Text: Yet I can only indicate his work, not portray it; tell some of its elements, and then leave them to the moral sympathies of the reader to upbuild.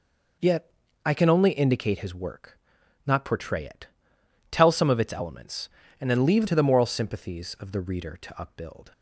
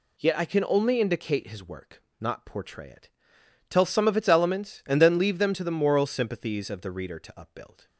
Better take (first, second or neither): second